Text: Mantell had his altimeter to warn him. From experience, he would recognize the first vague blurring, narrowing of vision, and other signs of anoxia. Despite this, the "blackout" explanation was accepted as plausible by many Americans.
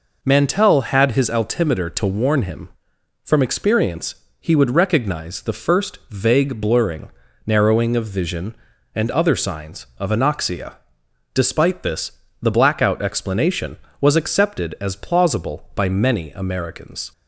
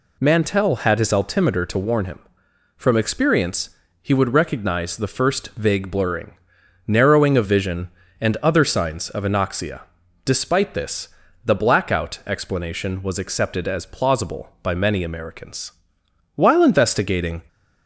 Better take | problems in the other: first | goes on to say "While investigating"; noticeable; from 16.3 s on; 1.0 s long

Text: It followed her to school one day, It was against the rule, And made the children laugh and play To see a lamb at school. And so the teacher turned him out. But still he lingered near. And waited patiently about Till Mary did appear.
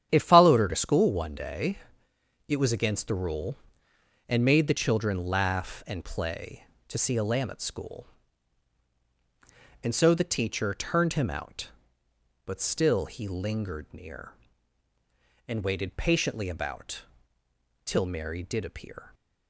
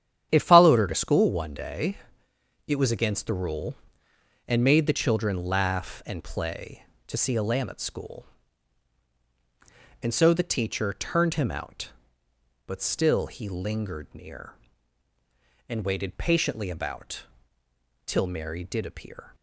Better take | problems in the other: neither | starts louder than the rest; strong; the same in both // pauses between "about" and "Till"; noticeable; the same in both

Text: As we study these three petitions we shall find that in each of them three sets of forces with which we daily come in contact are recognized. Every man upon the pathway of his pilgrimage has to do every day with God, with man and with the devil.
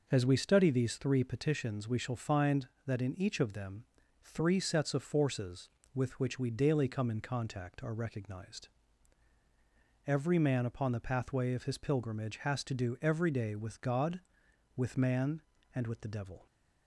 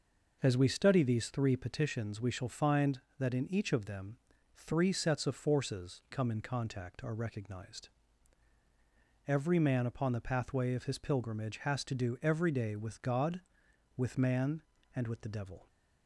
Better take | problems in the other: first | pauses between "them" and "three"; slight; at 4.1 s; 0.36 s long; slight in the first // skips "with which we daily"; at 6.0 s

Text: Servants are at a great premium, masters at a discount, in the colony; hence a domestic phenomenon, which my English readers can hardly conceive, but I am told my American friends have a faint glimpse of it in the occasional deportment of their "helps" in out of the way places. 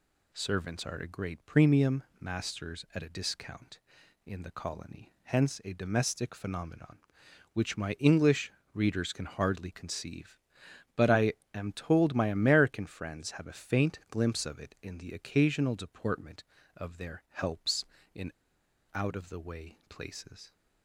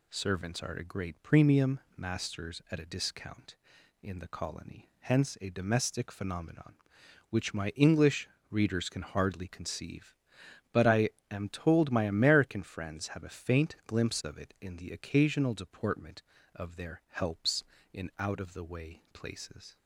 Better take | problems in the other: second | pauses between "English" and "readers"; slight; at 8.5 s; 0.22 s long; slight in the second // pauses between "I" and "am"; slight; at 11.3 s; 0.20 s long; slight in the second // pauses between "in" and "out"; noticeable; at 18.3 s; 0.62 s long

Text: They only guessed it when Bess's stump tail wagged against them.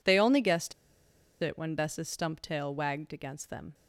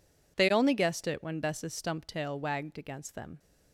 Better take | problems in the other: second | pauses between "guessed" and "it"; noticeable; at 0.7 s; 0.68 s long

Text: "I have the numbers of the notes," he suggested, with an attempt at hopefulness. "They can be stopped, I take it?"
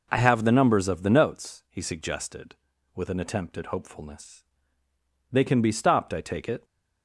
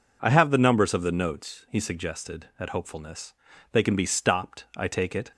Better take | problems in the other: first | skips "with an attempt"; at 2.5 s

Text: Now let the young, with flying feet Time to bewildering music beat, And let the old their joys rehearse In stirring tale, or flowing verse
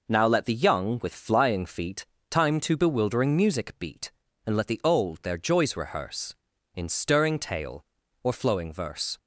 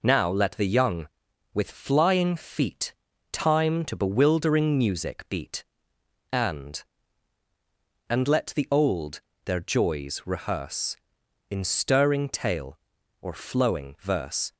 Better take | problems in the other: first | pauses between "feet" and "Time"; at 2.9 s; 0.40 s long; slight in the first // says "And" twice; at 8.0 s // pauses between "old" and "their"; slight; at 9.2 s; 0.24 s long

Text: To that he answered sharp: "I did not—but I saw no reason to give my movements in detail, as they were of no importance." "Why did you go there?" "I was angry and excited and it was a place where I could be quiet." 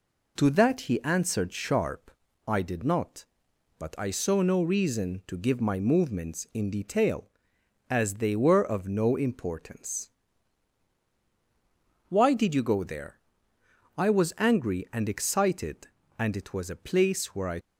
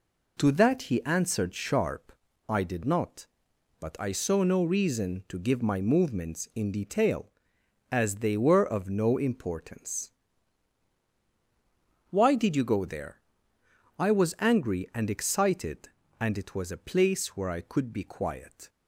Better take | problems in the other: second | stops before "could be quiet"; at 17.6 s

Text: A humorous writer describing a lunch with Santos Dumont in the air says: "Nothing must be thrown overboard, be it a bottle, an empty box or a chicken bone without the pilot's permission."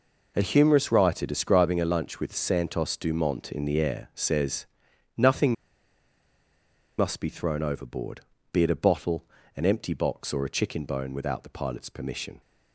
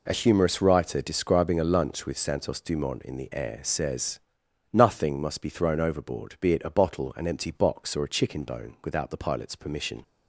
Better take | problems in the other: second | pauses between "Nothing" and "must"; strong; at 5.5 s; 1.4 s long

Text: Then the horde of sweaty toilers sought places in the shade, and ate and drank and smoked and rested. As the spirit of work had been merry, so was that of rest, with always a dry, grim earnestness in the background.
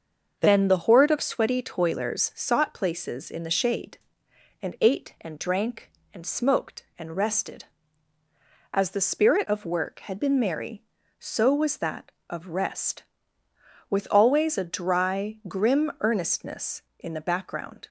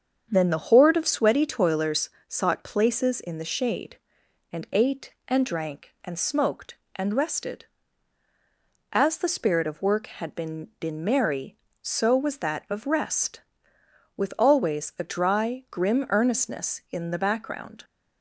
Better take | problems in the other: first | starts louder than the rest; strong; until 1.3 s; 7.5 dB; also in the first // pauses between "toilers" and "sought"; slight; at 2.0 s; 0.18 s long // says "been" twice; at 10.7 s

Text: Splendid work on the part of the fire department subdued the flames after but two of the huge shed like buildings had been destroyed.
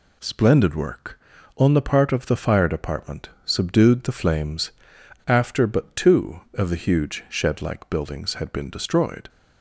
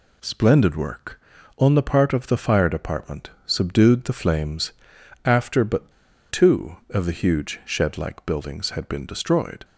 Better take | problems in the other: first | pauses between "department" and "subdued"; slight; at 3.2 s; 0.16 s long; slight in the first // pauses between "flames" and "after"; noticeable; at 4.7 s; 0.52 s long; noticeable in the first // pauses between "but" and "two"; at 5.9 s; 0.40 s long

